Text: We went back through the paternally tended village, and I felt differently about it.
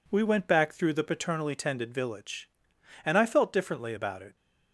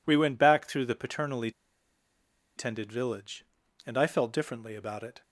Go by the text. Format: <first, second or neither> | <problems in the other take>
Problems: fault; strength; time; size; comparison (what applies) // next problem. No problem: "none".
first | pauses between "paternally" and "tended"; at 1.4 s; 1.0 s long